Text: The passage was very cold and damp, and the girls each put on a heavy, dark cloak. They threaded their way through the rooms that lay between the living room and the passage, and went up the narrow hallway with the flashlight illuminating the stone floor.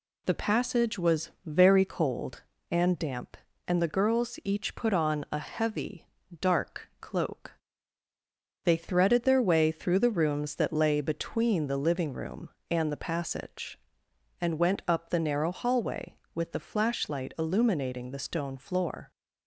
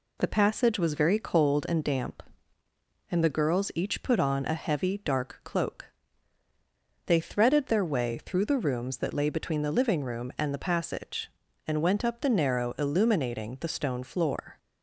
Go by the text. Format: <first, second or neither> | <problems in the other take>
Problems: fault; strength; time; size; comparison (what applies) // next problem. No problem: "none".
first | skips "hallway with the flashlight"; at 12.7 s